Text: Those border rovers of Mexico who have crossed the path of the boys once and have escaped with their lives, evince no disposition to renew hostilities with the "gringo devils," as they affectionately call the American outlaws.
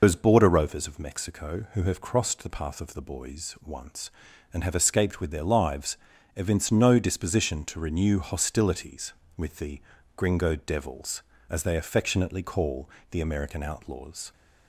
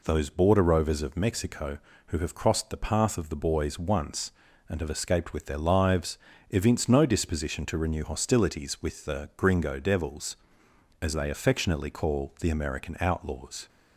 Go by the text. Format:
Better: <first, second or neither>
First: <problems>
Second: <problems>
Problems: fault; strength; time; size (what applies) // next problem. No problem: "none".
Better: second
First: loses the start of "Those"; at 0.0 s; 110 ms // pauses between "the" and "gringo"; slight; at 9.8 s; 0.34 s long // pauses between "call" and "the"; slight; at 12.8 s; 0.22 s long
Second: none